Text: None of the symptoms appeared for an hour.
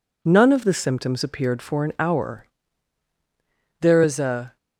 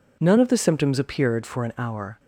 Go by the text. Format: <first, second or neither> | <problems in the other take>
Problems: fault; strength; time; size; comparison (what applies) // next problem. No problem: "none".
second | goes on to say "There is a"; noticeable; from 3.8 s on; 0.75 s long